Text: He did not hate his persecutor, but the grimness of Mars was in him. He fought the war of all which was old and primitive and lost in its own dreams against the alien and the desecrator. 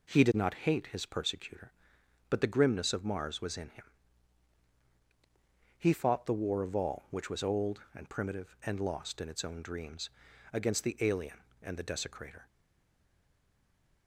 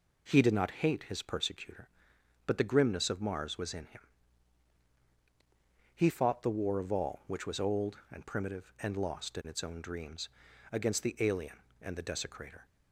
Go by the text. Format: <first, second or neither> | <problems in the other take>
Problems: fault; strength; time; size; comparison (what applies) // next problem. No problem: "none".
second | pauses between "dreams" and "against"; at 10.0 s; 0.42 s long; also in the second // stays silent after the last word; noticeable; from 12.4 s on; 1.6 s long